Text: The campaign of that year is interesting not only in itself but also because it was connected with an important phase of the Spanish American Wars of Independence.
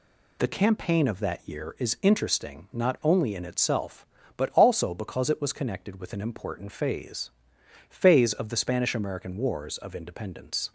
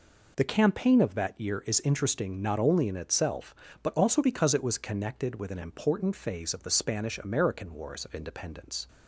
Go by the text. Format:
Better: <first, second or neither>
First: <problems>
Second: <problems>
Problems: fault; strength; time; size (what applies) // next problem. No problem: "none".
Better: second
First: says "phase" twice; at 7.8 s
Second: none